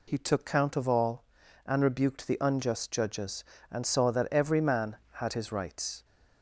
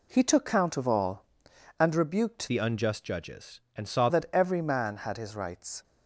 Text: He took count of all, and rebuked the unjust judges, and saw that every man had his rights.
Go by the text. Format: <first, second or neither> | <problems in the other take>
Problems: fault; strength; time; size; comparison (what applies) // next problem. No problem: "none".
first | changes voice from "the" to "saw"; from 2.4 to 4.0 s; 1.6 s long